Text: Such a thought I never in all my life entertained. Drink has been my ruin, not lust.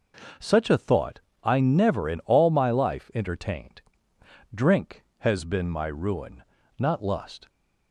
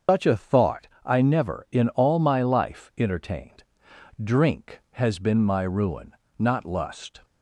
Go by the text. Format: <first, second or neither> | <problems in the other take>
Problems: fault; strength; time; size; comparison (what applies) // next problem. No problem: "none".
first | loses the start of "Such"; at 0.0 s; 145 ms // starts louder than the rest; until 1.2 s; 6.5 dB // pauses between "thought" and "I"; slight; at 0.8 s; 0.18 s long; slight in the first